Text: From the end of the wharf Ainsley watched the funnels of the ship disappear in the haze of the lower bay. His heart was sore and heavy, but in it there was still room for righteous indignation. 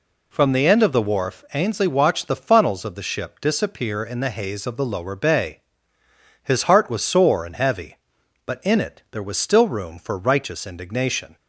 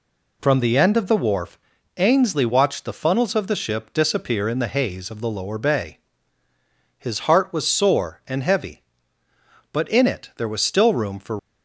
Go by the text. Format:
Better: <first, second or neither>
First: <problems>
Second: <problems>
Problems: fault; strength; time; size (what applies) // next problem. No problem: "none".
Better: first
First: none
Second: pauses between "wharf" and "Ainsley"; at 1.5 s; 0.38 s long // stops before "righteous indignation"; at 11.3 s